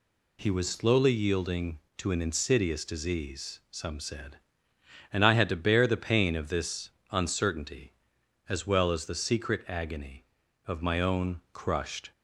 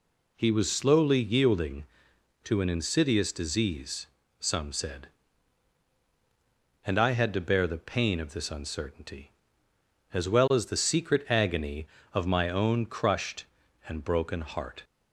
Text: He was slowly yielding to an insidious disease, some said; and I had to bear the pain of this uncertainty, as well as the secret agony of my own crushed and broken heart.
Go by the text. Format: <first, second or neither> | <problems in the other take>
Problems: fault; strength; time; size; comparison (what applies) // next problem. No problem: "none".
second | pauses between "this" and "uncertainty"; slight; at 6.9 s; 0.20 s long // stops before "and broken heart"; at 12.1 s